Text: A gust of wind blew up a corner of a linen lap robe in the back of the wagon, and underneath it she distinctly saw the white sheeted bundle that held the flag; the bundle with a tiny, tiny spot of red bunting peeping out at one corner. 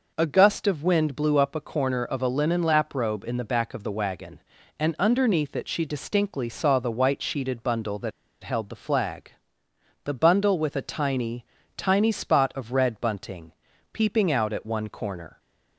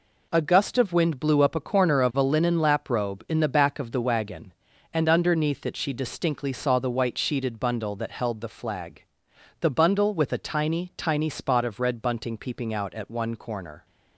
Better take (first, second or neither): second